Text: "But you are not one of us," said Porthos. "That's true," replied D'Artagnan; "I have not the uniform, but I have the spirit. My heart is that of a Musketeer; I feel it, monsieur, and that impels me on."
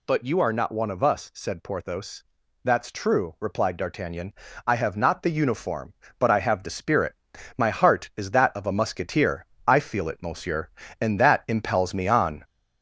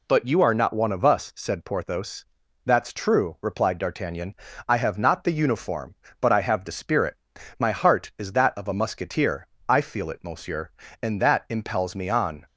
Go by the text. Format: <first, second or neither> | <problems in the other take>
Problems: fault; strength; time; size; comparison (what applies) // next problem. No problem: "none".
second | gets louder; noticeable; throughout; 4 dB